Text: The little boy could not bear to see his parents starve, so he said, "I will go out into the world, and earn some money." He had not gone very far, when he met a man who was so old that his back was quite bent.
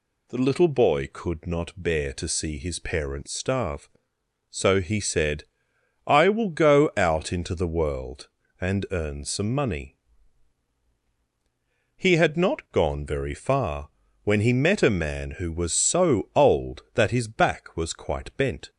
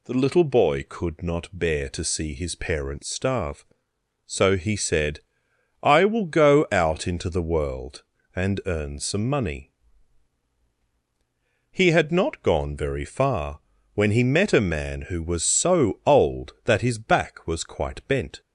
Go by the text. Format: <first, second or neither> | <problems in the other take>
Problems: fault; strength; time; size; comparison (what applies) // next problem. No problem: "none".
neither | none